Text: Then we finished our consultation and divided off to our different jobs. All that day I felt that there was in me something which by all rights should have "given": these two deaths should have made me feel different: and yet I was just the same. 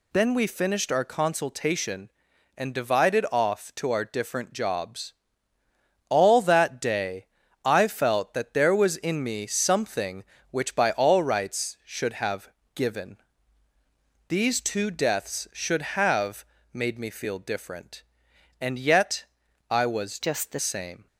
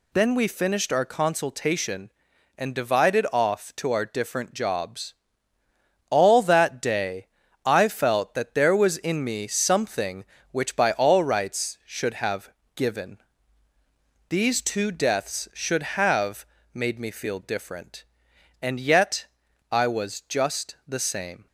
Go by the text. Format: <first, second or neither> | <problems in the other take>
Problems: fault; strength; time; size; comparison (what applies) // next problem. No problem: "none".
second | pauses between "day" and "I"; at 7.2 s; 0.38 s long; also in the second // pauses between "have" and "given"; slight; at 12.4 s; 0.26 s long; slight in the second // pauses between "have" and "made"; slight; at 16.4 s; 0.30 s long; slight in the second // pauses between "yet" and "I"; noticeable; at 19.2 s; 0.46 s long; noticeable in the second // changes voice from "just" to "the"; from 20.2 to 20.5 s; 0.3 s long